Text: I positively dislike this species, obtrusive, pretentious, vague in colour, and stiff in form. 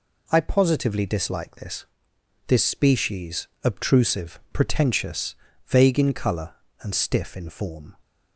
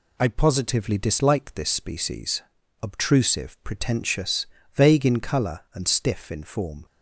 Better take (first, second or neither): second